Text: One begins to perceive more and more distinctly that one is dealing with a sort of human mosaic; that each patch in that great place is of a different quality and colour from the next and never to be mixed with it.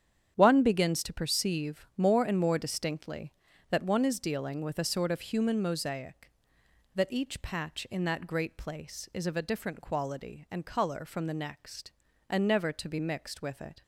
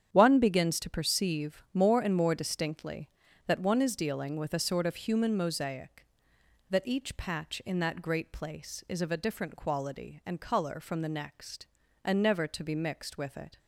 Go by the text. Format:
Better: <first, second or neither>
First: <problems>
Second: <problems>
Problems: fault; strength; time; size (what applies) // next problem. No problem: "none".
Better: neither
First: starts louder than the rest; strong; until 1.3 s; 9 dB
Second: starts louder than the rest; strong; until 1.1 s; 9 dB